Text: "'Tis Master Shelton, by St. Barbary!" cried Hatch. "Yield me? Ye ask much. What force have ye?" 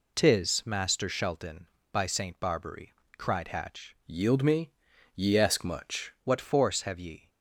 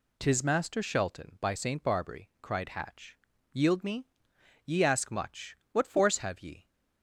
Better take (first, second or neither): second